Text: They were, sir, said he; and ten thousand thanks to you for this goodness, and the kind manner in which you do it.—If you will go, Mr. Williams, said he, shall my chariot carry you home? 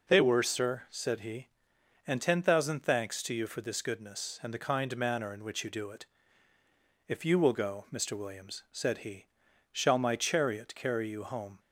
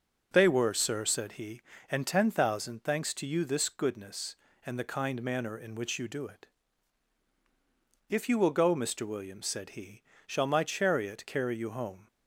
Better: first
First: none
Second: starts louder than the rest; noticeable; until 1.3 s; 6 dB // skips "for"; at 3.4 s

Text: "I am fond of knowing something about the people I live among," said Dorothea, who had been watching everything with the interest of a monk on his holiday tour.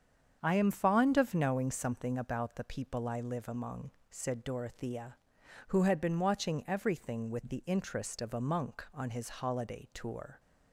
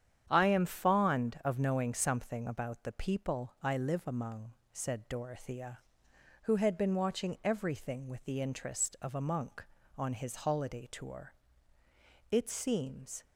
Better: first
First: starts louder than the rest; strong; until 1.4 s; 7.5 dB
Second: starts louder than the rest; strong; until 1.3 s; 9 dB // goes on to say "It seems"; noticeable; from 12.2 s on; 0.94 s long

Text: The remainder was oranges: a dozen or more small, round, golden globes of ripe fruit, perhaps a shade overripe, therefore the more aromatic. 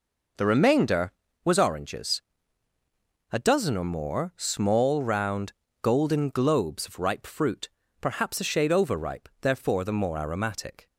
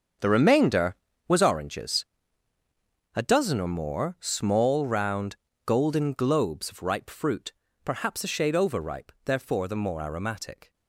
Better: first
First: none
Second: gets quieter; strong; throughout; 12.5 dB

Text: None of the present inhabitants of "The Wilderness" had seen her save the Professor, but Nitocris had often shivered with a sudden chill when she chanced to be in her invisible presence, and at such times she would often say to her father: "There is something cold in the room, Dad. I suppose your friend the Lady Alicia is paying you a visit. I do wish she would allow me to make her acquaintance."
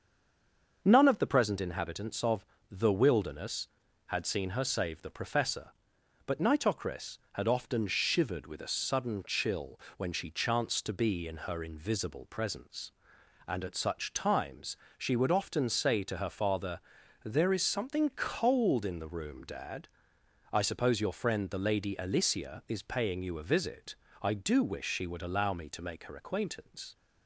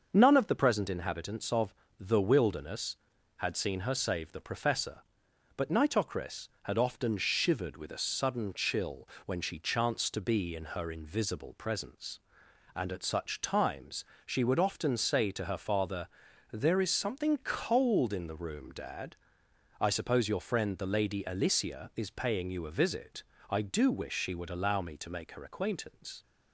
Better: second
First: stays silent before the first word; slight; until 0.8 s; 0.8 s long // starts louder than the rest; until 1.8 s; 6.5 dB // pauses between "of" and "The"; slight; at 2.4 s; 0.26 s long // pauses between "chill" and "when"; slight; at 9.8 s; 0.16 s long // pauses between "times" and "she"; slight; at 14.7 s; 0.22 s long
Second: starts louder than the rest; until 1.1 s; 6.5 dB // pauses between "of" and "The"; slight; at 1.7 s; 0.26 s long // pauses between "chill" and "when"; slight; at 9.0 s; 0.16 s long // pauses between "times" and "she"; slight; at 14.0 s; 0.22 s long

